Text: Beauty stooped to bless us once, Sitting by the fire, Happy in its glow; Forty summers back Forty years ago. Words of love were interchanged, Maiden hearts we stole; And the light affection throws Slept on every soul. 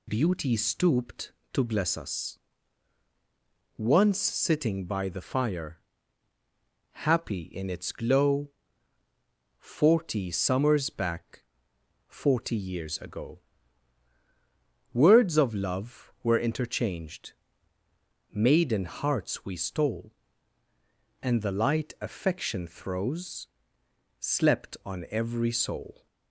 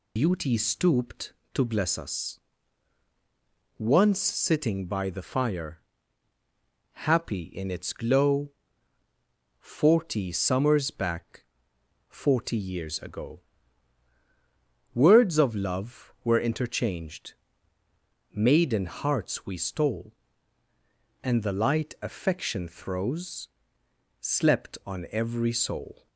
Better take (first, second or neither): first